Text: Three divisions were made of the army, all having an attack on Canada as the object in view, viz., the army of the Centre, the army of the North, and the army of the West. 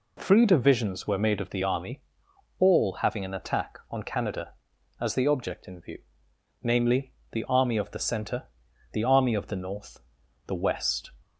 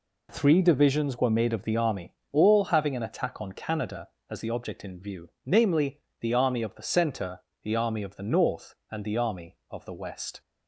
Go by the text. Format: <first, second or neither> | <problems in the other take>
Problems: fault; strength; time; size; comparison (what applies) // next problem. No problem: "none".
second | skips "and the army of"; at 10.2 s